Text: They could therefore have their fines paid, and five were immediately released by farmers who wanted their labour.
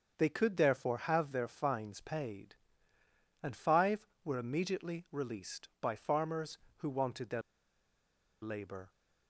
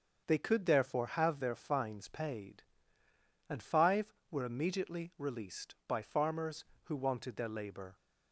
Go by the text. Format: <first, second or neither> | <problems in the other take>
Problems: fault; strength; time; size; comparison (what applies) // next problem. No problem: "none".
second | starts louder than the rest; until 1.1 s; 6.5 dB; also in the second // pauses between "their" and "labour"; at 7.4 s; 1.0 s long